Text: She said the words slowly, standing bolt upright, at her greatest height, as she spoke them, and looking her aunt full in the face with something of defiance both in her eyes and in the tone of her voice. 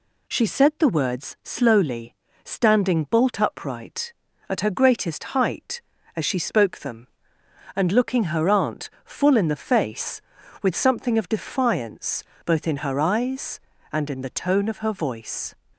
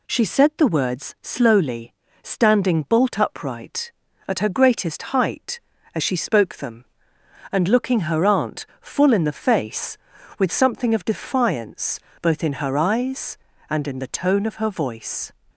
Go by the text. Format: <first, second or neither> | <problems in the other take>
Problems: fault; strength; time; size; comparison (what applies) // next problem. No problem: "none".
neither | pauses between "aunt" and "full"; slight; the same in both // pauses between "defiance" and "both"; slight; the same in both